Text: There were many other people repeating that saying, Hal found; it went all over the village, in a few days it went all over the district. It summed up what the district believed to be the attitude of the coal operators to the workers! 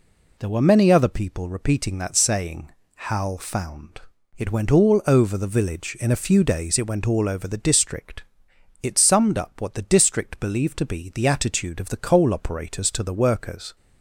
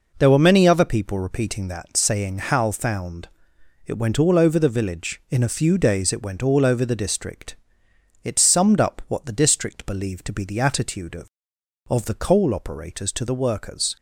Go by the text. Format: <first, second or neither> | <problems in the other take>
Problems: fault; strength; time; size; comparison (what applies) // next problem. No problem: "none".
first | says "of" twice; at 11.8 s